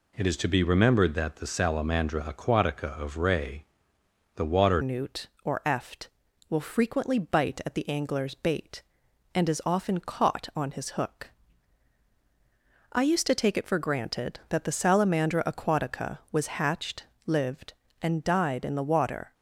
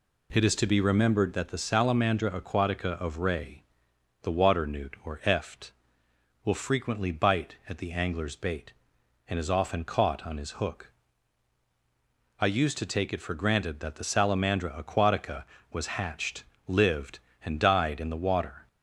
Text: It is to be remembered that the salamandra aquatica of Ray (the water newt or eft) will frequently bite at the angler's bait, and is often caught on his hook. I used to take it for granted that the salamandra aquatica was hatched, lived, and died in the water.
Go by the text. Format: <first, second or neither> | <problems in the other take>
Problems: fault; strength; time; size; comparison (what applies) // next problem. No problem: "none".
second | changes voice at "newt"; from 4.8 s on; 14.5 s long